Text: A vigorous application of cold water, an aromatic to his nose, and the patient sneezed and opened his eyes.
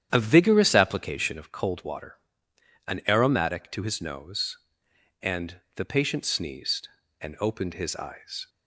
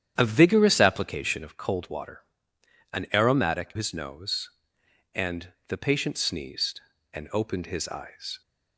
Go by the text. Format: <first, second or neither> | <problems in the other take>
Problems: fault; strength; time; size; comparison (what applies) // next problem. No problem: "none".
first | starts louder than the rest; strong; until 1.1 s; 9.5 dB; strong in the first // skips "to"; at 3.7 s // pauses between "and" and "the"; slight; at 5.4 s; 0.18 s long; slight in the first